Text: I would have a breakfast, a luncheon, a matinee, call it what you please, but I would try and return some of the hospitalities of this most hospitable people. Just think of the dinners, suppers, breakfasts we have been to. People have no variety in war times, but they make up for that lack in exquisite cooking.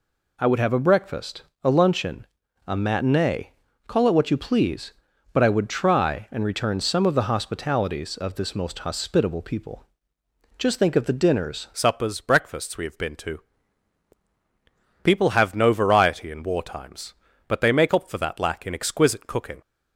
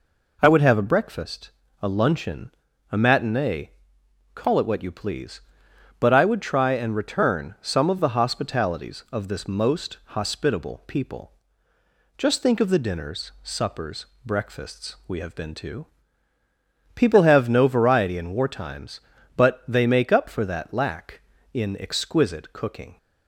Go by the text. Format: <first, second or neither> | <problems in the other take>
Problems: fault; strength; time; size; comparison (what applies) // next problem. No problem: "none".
second | changes voice at "suppers"; from 11.7 s on; 7.9 s long